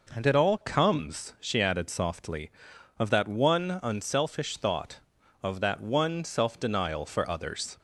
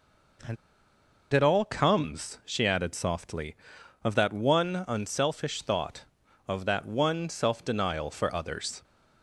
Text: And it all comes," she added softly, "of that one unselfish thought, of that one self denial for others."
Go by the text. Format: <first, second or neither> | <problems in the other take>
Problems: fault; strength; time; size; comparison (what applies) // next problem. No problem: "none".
first | pauses between "And" and "it"; noticeable; at 0.5 s; 0.76 s long